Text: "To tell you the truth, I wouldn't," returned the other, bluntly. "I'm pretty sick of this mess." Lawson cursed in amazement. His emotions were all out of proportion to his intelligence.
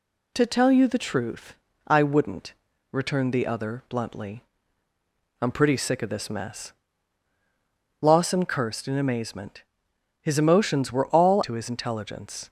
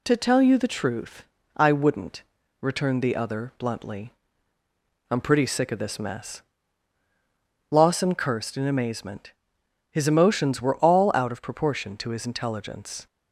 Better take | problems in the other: second | skips "out of proportion"; at 11.4 s

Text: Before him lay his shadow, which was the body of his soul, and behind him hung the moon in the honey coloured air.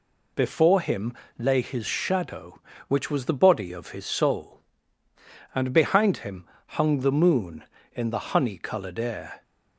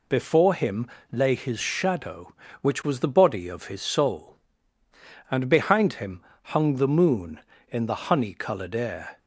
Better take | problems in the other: neither | pauses between "him" and "lay"; slight; the same in both // pauses between "him" and "hung"; slight; the same in both

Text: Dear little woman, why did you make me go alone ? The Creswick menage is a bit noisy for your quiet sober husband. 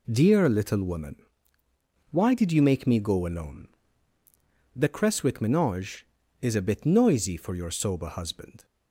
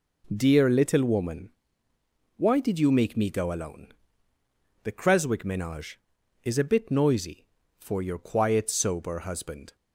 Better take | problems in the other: second | skips "quiet"; at 7.7 s

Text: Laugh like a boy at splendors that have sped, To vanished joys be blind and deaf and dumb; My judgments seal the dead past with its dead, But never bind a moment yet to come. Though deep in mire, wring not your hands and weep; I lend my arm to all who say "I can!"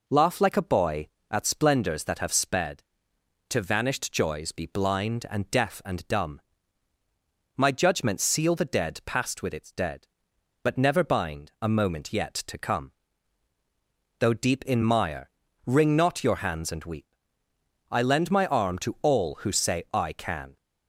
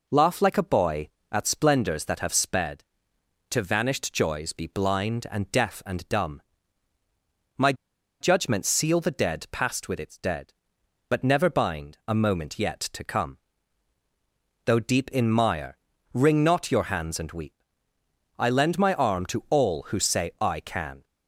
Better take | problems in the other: first | pauses between "My" and "judgments"; noticeable; at 7.7 s; 0.47 s long

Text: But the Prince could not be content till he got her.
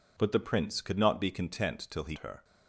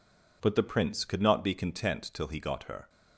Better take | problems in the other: second | skips "got"; at 2.1 s

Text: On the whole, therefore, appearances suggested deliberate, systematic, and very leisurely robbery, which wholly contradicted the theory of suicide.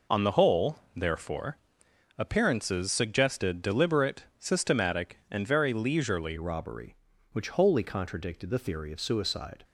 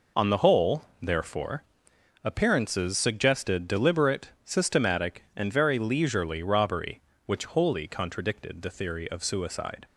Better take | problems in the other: second | changes voice at "robbery"; from 6.3 s on; 3.3 s long

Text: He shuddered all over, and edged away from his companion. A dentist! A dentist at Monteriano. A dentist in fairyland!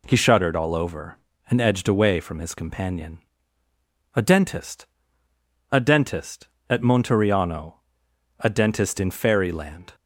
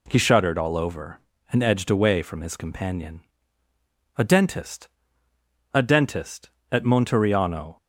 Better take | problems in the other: first | stops before "A dentist in fairyland"; at 7.7 s

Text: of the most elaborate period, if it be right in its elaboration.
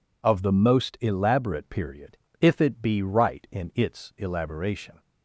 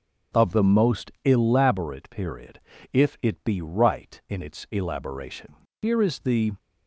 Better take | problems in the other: first | goes on to say "Here is the"; noticeable; from 5.8 s on; 0.72 s long

